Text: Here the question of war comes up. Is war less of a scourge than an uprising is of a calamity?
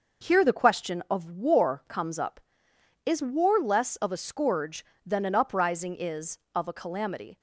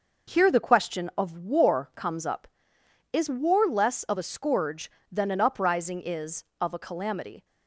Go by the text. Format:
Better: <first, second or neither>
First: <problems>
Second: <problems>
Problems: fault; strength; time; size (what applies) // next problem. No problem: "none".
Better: neither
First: none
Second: none